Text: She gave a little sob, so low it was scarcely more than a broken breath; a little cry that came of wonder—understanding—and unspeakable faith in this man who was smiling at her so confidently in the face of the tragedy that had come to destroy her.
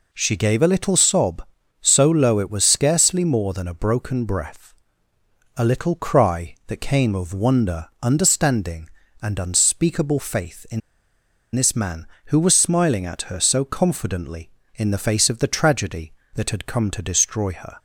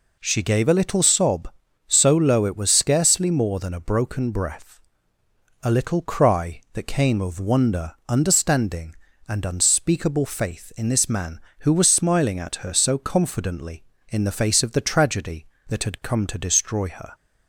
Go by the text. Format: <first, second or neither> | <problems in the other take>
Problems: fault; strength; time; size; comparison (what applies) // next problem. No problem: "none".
second | pauses between "in" and "this"; noticeable; at 10.8 s; 0.74 s long